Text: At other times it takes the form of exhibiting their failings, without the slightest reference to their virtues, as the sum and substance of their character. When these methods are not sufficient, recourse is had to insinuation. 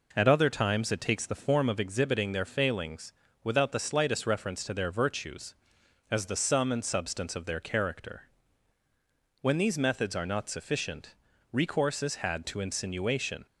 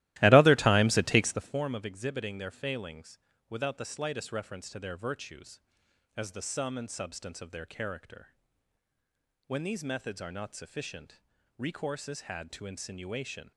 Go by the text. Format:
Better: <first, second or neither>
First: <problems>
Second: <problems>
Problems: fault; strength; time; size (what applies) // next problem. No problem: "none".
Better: first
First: none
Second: starts louder than the rest; strong; until 1.6 s; 16.5 dB